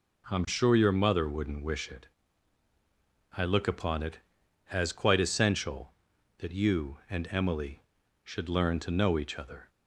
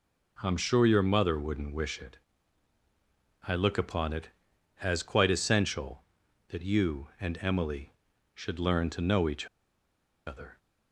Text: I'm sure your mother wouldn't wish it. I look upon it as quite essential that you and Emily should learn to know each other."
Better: first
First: none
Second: pauses between "each" and "other"; noticeable; at 9.4 s; 0.79 s long

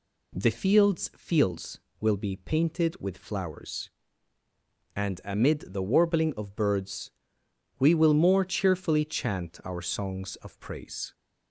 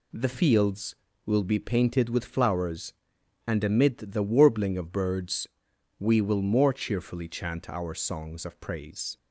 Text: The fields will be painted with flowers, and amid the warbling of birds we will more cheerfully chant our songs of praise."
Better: second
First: says "fields" twice; at 1.1 s // pauses between "birds" and "we"; noticeable; at 7.1 s; 0.66 s long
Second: pauses between "birds" and "we"; noticeable; at 5.4 s; 0.52 s long

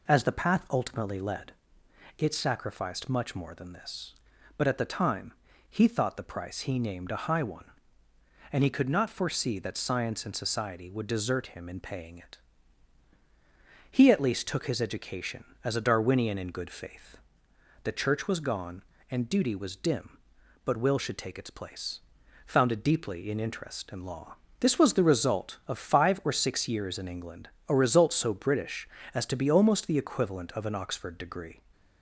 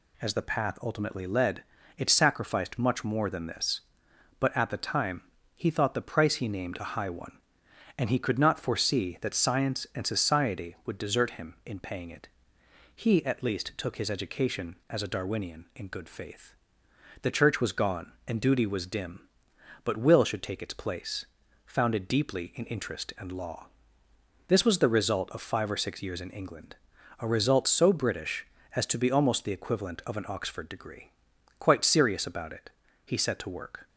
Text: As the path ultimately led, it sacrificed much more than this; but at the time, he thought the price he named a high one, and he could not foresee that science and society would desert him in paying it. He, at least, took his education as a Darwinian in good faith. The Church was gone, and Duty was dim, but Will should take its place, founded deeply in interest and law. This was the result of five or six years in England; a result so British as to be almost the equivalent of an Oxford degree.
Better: first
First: none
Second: goes on to say "Quite serious about it he set to work"; strong; from 31.5 s on; 2.2 s long

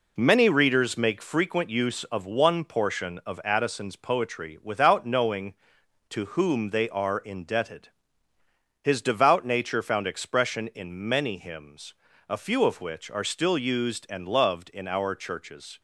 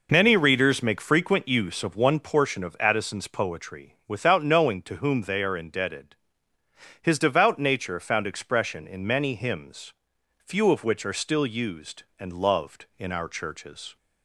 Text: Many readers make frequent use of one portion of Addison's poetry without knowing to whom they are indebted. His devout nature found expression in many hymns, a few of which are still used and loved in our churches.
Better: first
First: none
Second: skips "a"; at 10.1 s

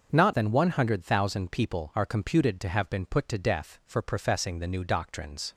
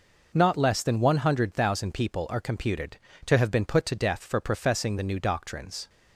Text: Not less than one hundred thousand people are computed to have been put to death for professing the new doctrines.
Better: second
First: starts louder than the rest; until 1.1 s; 6.5 dB // skips "less"; at 0.3 s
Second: none

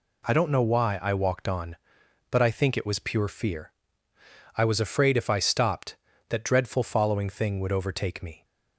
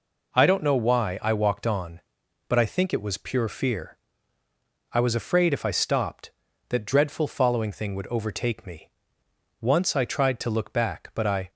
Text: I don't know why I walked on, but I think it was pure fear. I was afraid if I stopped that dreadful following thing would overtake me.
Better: first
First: none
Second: goes on to say "Once I tried to look back but I"; strong; from 9.5 s on; 1.9 s long

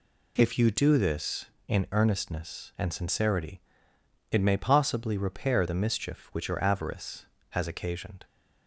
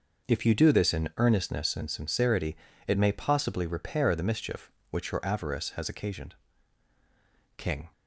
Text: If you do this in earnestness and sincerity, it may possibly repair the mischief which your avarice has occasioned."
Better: first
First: none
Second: goes on to say "King"; slight; from 7.5 s on; 0.34 s long

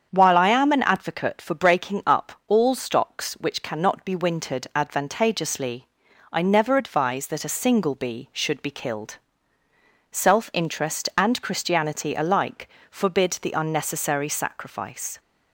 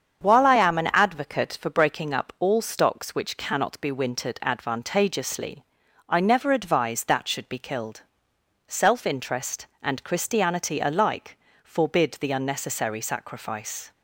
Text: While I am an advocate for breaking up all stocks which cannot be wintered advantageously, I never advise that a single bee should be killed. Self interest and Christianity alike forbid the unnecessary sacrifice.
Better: first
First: starts louder than the rest; strong; until 1.1 s; 7.5 dB // pauses between "alike" and "forbid"; slight; at 12.6 s; 0.20 s long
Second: starts louder than the rest; strong; until 1.2 s; 7.5 dB // skips "a single bee"; at 7.2 s // pauses between "alike" and "forbid"; slight; at 11.3 s; 0.24 s long

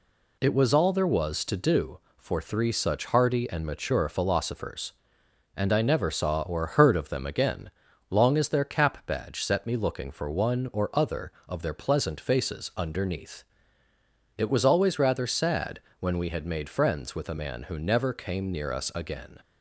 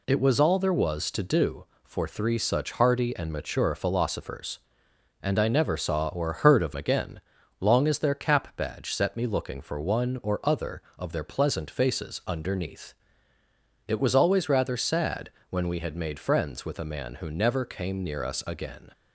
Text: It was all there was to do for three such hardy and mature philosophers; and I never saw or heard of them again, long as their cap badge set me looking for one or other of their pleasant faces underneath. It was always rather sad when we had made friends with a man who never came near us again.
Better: first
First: pauses between "sad" and "when"; slight; at 15.7 s; 0.20 s long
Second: skips "them"; at 6.7 s // pauses between "sad" and "when"; slight; at 15.2 s; 0.20 s long

